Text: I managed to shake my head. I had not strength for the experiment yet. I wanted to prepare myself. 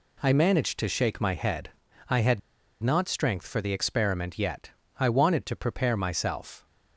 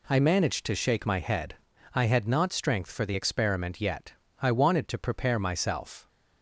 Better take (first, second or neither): second